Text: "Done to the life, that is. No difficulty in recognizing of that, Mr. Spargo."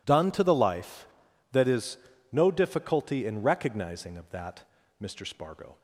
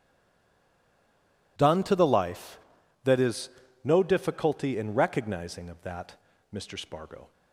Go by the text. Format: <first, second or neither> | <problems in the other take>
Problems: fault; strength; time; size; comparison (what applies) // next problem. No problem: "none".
first | stays silent before the first word; noticeable; until 1.5 s; 1.5 s long